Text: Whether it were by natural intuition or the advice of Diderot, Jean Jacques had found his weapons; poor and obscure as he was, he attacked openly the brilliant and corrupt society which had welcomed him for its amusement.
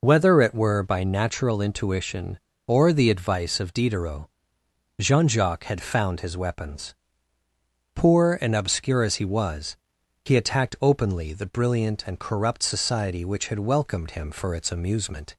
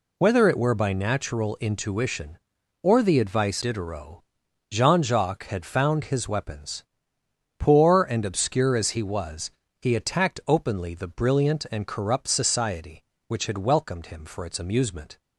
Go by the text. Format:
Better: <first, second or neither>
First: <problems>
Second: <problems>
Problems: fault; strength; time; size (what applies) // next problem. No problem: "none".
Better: first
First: none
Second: skips "of"; at 3.6 s